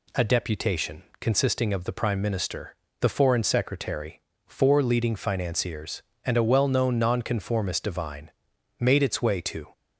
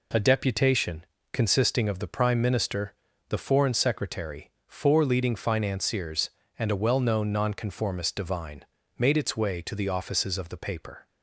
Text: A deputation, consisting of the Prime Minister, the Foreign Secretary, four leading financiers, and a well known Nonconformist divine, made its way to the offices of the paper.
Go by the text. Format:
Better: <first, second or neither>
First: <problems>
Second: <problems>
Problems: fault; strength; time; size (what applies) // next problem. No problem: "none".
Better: second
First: stops before "the offices of the paper"; at 9.7 s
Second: none